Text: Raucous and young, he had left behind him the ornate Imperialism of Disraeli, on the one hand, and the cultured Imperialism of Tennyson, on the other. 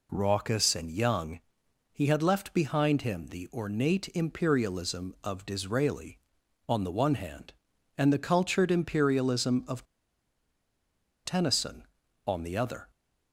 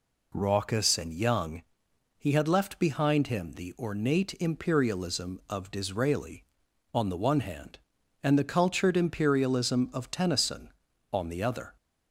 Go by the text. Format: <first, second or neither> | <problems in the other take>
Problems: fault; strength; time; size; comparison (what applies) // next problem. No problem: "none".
second | pauses between "of" and "Tennyson"; strong; at 9.8 s; 1.4 s long